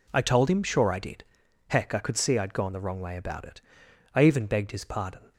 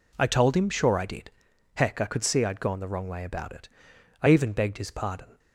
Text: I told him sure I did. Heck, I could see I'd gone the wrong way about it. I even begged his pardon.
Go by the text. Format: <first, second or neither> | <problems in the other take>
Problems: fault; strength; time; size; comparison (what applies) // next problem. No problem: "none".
neither | none